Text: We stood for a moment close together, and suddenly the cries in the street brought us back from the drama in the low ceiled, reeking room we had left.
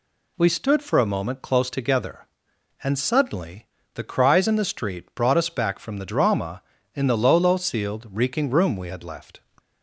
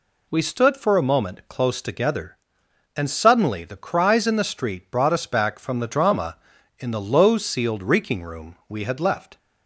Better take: second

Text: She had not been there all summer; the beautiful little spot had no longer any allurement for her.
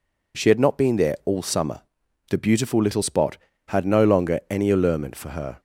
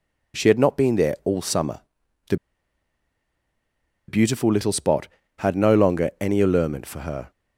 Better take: first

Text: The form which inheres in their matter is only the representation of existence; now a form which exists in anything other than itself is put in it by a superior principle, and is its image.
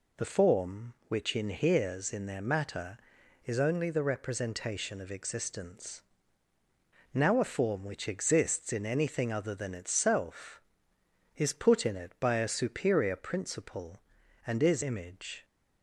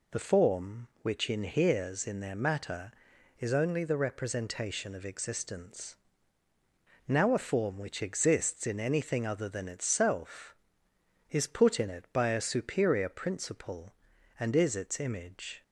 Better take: second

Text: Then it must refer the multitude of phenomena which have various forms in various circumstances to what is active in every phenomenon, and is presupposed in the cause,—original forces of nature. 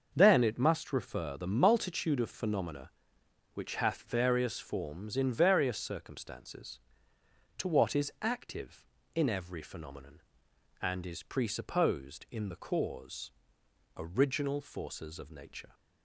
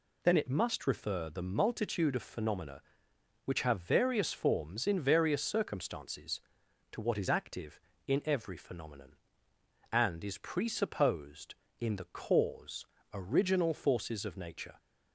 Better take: second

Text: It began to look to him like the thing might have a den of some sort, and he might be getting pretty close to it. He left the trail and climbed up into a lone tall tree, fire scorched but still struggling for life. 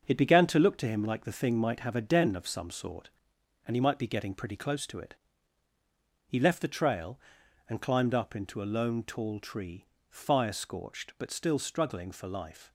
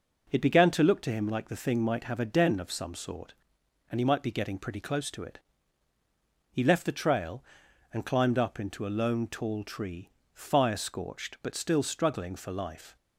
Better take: second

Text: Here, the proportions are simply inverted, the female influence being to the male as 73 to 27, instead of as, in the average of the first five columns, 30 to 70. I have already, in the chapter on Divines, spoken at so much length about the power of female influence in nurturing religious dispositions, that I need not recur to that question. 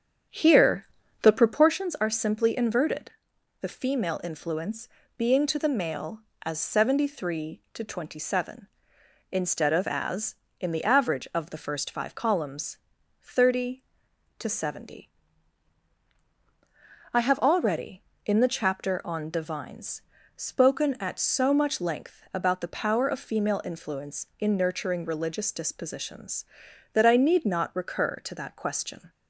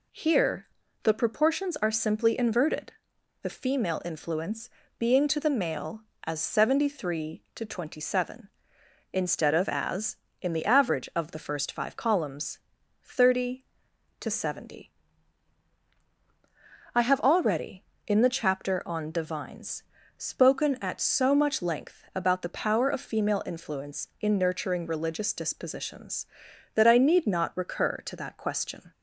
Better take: second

